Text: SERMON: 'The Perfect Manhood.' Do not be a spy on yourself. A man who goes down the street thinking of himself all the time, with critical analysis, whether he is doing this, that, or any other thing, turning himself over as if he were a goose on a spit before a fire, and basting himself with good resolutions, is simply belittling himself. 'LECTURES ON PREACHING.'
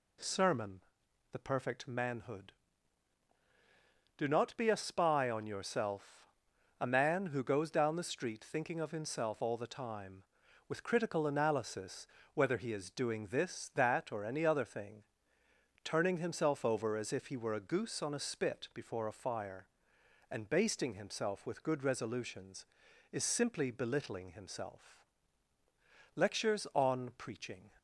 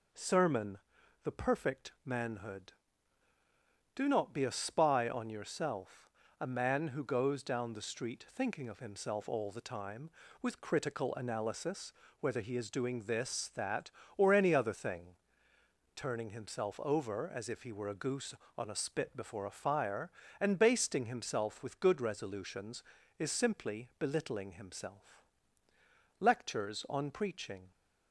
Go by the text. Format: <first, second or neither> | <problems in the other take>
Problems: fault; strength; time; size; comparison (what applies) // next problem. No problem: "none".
neither | none